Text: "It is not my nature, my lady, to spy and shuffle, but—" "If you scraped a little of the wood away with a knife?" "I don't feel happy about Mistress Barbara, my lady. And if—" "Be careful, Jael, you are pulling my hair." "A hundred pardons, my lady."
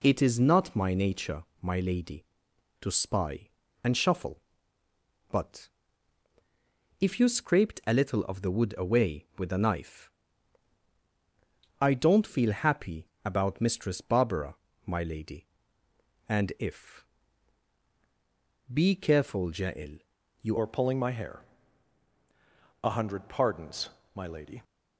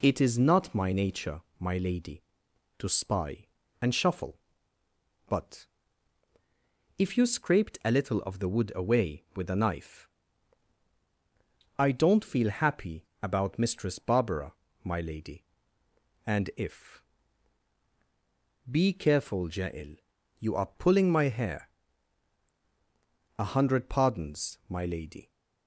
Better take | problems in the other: second | pauses between "happy" and "about"; slight; at 13.0 s; 0.18 s long; slight in the second // changes voice at "are"; from 20.5 s on; 4.1 s long

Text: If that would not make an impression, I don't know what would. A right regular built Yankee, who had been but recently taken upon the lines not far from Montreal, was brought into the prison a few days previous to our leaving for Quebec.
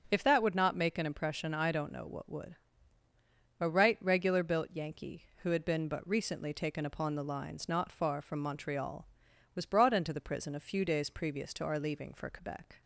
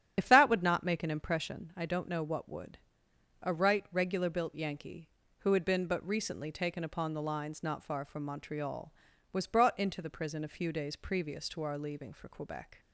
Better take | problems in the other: first | loses the start of "If"; at 0.1 s; 60 ms // starts louder than the rest; strong; until 1.1 s; 9 dB

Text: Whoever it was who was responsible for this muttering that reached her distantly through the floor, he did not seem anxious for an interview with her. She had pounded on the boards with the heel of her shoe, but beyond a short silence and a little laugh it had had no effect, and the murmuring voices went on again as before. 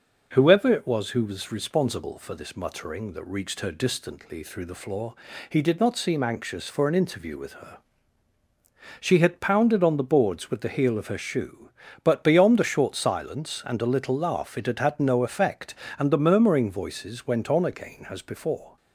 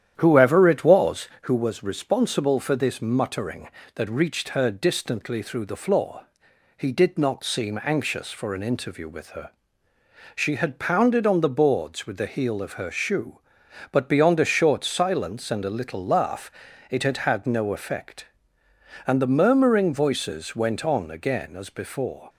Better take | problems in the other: first | starts louder than the rest; strong; until 1.5 s; 10 dB // pauses between "laugh" and "it"; at 16.5 s; 0.40 s long

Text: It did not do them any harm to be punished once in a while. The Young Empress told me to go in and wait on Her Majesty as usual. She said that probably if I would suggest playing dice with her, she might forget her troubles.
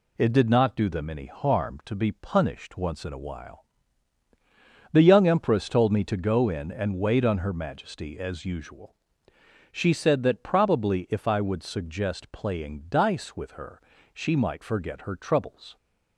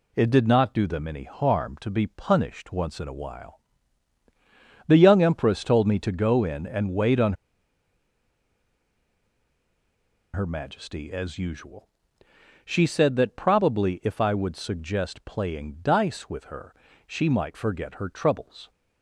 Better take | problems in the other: first | pauses between "on" and "Her"; strong; at 7.3 s; 3.0 s long

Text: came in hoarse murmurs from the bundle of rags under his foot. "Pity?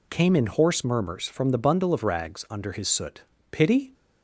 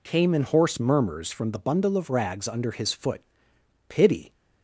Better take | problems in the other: second | says "soot" for "foot"; at 2.8 s

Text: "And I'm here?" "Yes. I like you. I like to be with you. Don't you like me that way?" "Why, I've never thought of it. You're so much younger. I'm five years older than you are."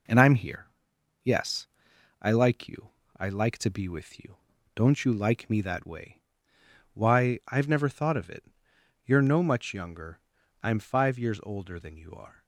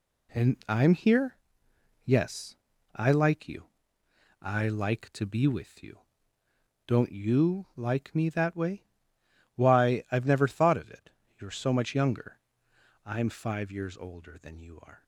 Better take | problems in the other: second | says "no" for "so"; at 9.2 s

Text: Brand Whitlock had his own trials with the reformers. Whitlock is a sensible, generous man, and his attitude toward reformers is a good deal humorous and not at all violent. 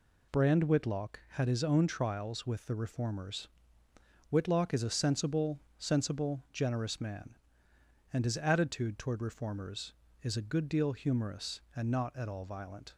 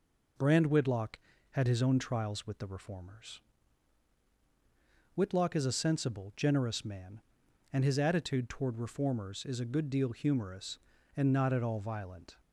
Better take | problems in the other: second | says "sensible" twice; at 5.8 s

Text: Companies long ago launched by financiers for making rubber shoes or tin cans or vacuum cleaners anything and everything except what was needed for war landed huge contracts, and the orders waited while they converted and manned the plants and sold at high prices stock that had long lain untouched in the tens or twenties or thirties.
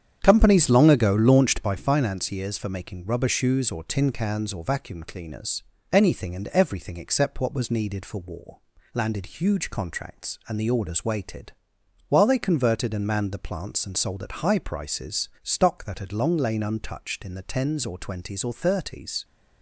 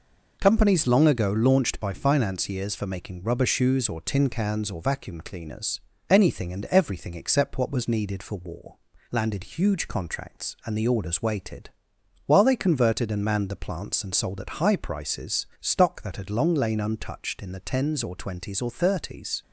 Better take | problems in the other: second | starts louder than the rest; strong; until 1.9 s; 8.5 dB // pauses between "cleaners" and "anything"; slight; at 5.6 s; 0.30 s long; slight in the second // pauses between "war" and "landed"; slight; at 8.5 s; 0.32 s long; slight in the second // pauses between "waited" and "while"; noticeable; at 11.5 s; 0.58 s long; noticeable in the second

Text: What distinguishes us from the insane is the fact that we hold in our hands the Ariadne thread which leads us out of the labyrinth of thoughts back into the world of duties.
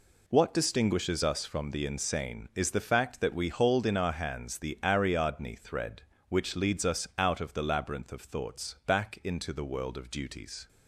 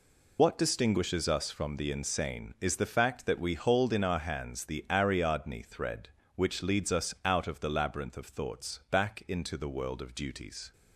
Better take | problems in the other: first | loses the start of "What"; at 0.3 s; 70 ms

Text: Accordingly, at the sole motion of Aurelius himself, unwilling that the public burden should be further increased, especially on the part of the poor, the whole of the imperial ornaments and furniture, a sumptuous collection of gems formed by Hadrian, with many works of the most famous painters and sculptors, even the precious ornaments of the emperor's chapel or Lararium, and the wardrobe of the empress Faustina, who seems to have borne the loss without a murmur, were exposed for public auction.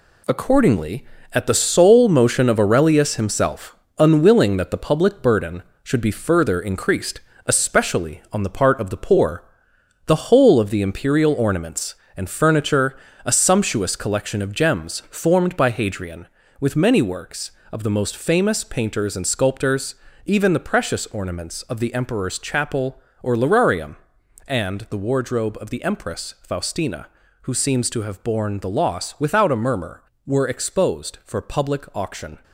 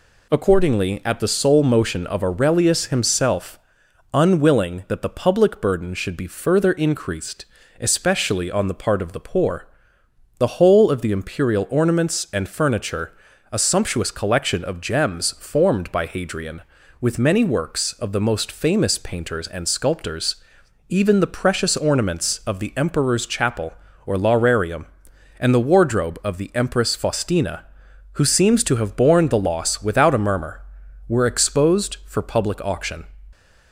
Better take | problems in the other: second | gets quieter; strong; throughout; 7.5 dB

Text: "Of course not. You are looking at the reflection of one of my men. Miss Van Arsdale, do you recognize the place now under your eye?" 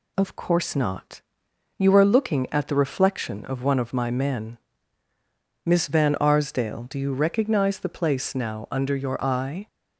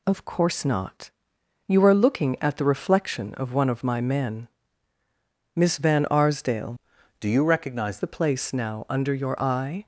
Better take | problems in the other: first | changes voice from "do" to "recognize"; from 7.1 to 7.9 s; 0.8 s long

